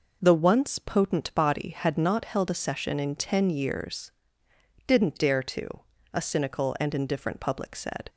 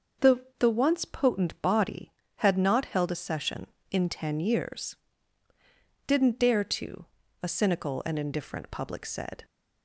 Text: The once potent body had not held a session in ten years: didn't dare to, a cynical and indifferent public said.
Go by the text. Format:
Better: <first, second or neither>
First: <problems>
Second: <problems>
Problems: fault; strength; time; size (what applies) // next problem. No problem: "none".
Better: first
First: none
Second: starts louder than the rest; until 1.3 s; 6 dB // says "The" twice; at 0.5 s